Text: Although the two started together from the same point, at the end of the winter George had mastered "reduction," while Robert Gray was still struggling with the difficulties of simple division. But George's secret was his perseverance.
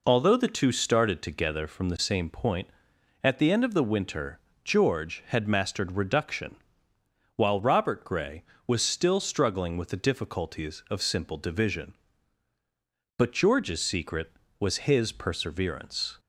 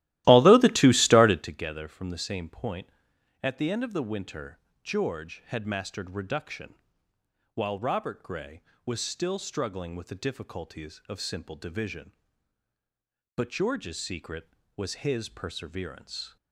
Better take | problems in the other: first | starts louder than the rest; strong; until 1.6 s; 16 dB // pauses between "winter" and "George"; slight; at 4.5 s; 0.26 s long; slight in the first

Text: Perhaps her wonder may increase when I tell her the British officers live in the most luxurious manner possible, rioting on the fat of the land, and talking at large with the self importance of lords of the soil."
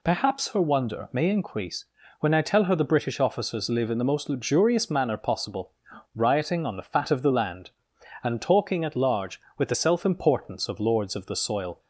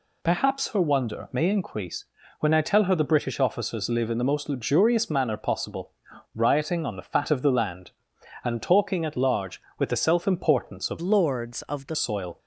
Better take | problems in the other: first | pauses between "increase" and "when"; slight; at 2.0 s; 0.34 s long; slight in the first // changes voice from "lords" to "the"; from 11.0 to 11.9 s; 0.9 s long

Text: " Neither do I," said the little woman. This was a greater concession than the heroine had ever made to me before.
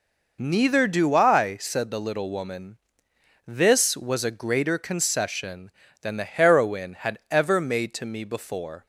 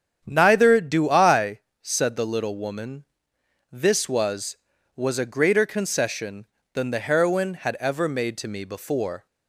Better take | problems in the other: first | starts louder than the rest; strong; until 1.2 s; 8 dB // says "was" twice; at 4.9 s

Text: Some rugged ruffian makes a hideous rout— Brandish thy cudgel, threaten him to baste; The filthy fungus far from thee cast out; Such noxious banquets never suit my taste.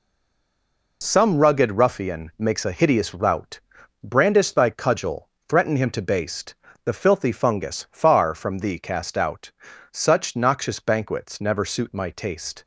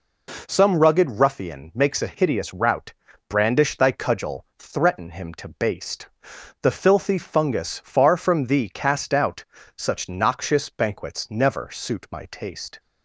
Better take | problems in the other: second | stays silent before the first word; until 1.0 s; 1.0 s long

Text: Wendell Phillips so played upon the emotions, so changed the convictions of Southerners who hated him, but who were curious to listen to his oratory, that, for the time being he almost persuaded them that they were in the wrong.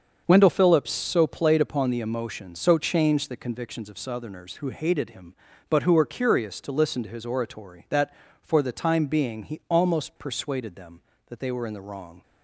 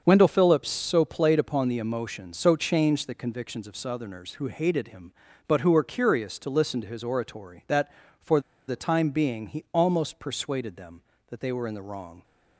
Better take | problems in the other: first | starts louder than the rest; until 1.0 s; 6.5 dB; also in the first // pauses between "for" and "the"; slight; at 8.4 s; 0.27 s long

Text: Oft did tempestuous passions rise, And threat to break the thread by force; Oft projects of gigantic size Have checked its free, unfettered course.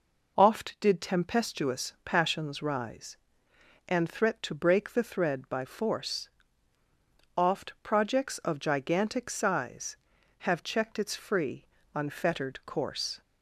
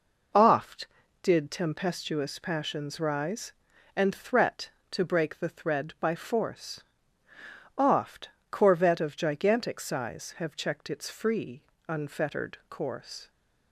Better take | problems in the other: first | says "corvette" for "projects"; at 8.5 s

